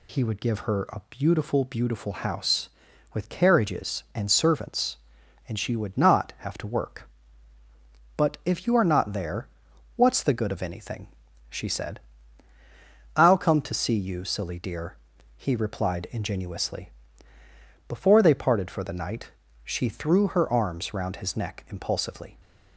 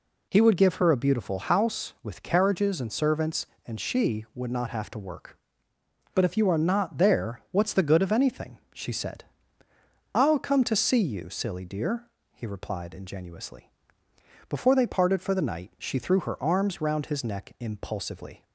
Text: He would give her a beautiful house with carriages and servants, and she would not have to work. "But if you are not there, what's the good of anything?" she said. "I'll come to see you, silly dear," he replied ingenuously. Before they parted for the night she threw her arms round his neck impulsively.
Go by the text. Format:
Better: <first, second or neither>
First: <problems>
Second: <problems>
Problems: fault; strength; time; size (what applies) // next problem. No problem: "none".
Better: second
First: says "beautiful" twice; at 1.6 s // pauses between "night" and "she"; slight; at 19.3 s; 0.32 s long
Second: none